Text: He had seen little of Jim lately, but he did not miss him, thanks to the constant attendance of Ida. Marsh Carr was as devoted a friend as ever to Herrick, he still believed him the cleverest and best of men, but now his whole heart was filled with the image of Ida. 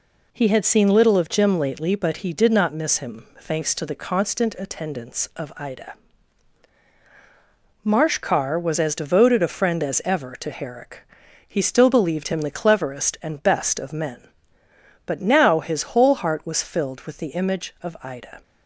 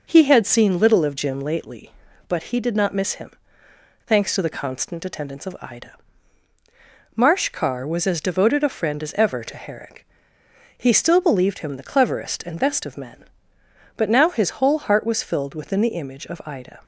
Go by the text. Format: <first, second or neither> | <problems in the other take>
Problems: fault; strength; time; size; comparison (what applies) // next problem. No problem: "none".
first | says "within" for "with"; at 15.5 s